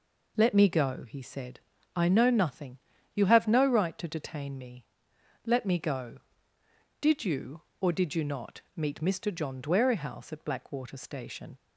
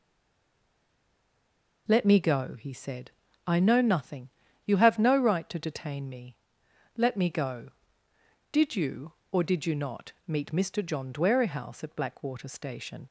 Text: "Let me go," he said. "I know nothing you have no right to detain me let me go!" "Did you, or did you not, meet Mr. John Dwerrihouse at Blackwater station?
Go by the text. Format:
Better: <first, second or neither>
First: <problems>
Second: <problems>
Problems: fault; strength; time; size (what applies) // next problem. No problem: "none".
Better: first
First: pauses between "nothing" and "you"; slight; at 2.7 s; 0.36 s long // pauses between "me" and "let"; noticeable; at 4.8 s; 0.62 s long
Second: stays silent before the first word; noticeable; until 1.8 s; 1.8 s long // pauses between "nothing" and "you"; slight; at 4.2 s; 0.36 s long // pauses between "me" and "let"; noticeable; at 6.3 s; 0.62 s long